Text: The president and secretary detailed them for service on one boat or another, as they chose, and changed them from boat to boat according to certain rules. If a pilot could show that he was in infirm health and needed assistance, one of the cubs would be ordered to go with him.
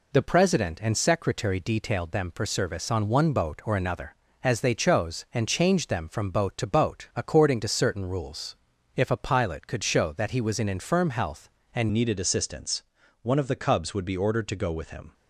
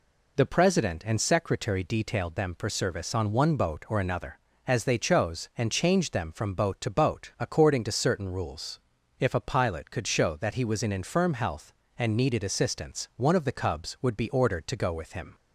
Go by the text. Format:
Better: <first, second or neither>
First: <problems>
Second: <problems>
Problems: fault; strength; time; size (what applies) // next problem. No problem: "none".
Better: second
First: changes voice at "needed"; from 11.9 s on; 3.2 s long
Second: none